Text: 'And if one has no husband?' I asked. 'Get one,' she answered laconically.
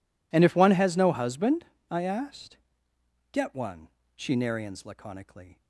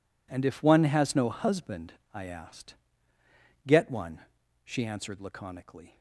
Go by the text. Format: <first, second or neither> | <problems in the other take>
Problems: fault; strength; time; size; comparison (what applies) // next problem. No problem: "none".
second | says "narians" for "answered"; at 4.3 s